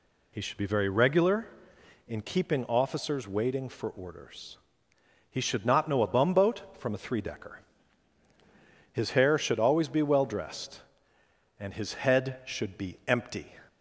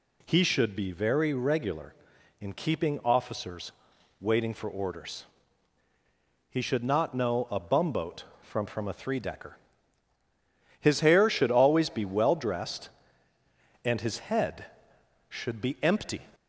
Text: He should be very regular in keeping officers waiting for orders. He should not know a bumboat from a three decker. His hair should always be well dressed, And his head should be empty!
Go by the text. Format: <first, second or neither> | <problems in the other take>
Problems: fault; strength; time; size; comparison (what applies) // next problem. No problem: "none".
first | pauses between "officers" and "waiting"; noticeable; at 3.7 s; 0.48 s long // says "from" twice; at 8.6 s